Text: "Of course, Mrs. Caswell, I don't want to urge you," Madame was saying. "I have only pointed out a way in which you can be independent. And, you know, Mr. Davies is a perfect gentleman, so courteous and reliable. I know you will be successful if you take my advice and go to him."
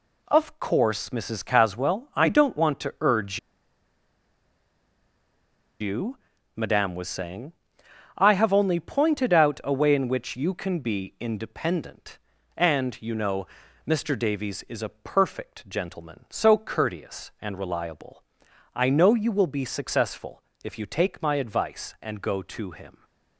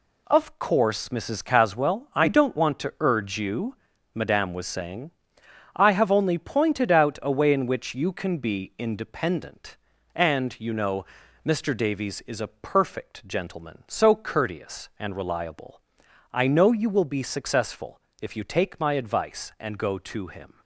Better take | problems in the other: second | pauses between "urge" and "you"; strong; at 3.3 s; 2.4 s long // pauses between "successful" and "if"; slight; at 20.4 s; 0.22 s long; slight in the second

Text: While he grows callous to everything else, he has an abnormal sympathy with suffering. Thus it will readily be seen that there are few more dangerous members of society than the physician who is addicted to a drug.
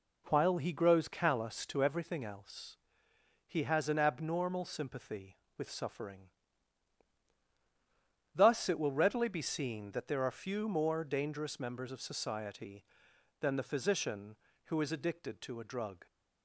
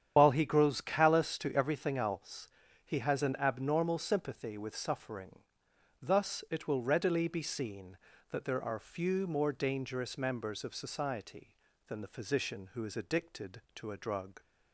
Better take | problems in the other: first | loses the start of "While"; at 0.1 s; 60 ms // starts louder than the rest; strong; until 1.1 s; 9 dB

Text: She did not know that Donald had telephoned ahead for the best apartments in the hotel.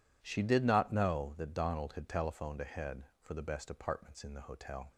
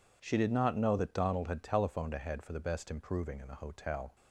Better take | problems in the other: first | says "improving" for "apartments"; at 2.9 s

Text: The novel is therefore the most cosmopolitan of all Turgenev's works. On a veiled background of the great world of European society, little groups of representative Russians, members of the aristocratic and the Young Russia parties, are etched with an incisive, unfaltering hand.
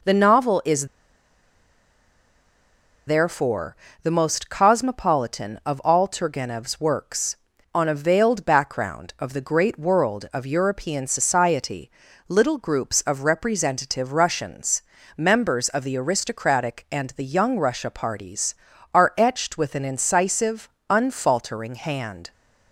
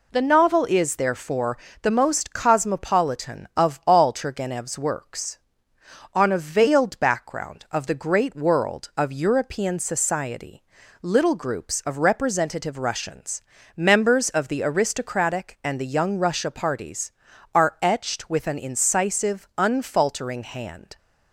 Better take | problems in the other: second | pauses between "is" and "therefore"; strong; at 0.8 s; 2.1 s long // pauses between "therefore" and "the"; slight; at 3.7 s; 0.26 s long; slight in the second

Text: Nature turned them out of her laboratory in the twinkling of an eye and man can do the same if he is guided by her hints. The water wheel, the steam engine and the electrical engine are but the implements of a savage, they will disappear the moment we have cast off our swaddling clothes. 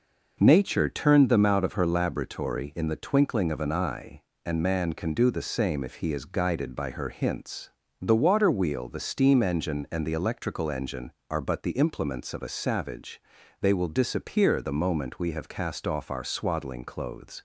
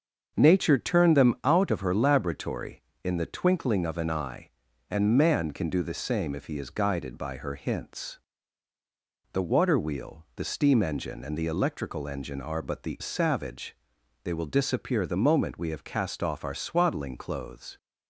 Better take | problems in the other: first | starts louder than the rest; until 1.3 s; 6.5 dB // skips "implements of a"; at 12.9 s

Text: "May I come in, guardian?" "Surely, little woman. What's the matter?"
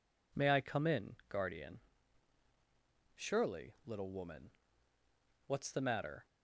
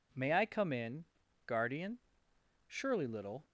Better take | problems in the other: first | stops before "woman What's the matter"; at 3.4 s

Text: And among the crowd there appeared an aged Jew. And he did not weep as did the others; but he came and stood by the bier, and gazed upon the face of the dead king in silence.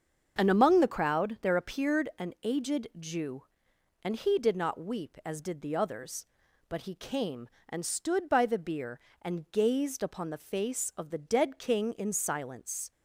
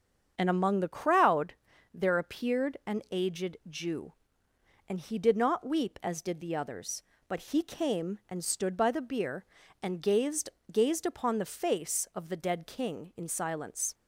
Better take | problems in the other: first | starts louder than the rest; until 1.3 s; 7 dB; also in the first // pauses between "crowd" and "there"; at 1.5 s; 0.40 s long // says "gazed" twice; at 10.7 s

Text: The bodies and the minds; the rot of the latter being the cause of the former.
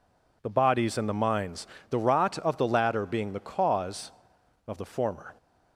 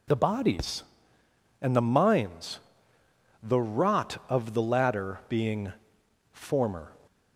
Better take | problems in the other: first | skips "the cause of the"; at 6.0 s

